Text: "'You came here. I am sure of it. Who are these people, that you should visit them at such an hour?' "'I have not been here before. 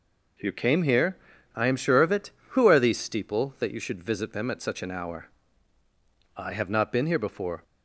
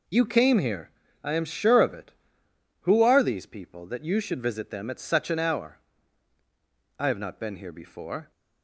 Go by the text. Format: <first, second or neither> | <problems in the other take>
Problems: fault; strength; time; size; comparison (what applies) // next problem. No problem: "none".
second | says "steeple" for "people"; at 2.9 s